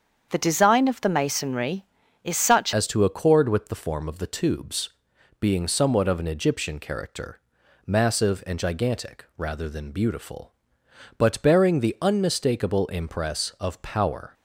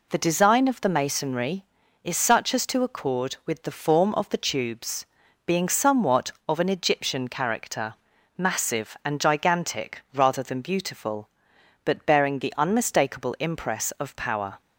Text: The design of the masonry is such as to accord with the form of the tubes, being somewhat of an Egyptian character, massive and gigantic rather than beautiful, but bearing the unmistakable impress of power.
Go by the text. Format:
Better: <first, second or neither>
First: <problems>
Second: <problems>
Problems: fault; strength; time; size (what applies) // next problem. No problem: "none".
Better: second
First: starts louder than the rest; strong; until 1.3 s; 7.5 dB // changes voice at "as"; from 2.7 s on; 11.6 s long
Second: none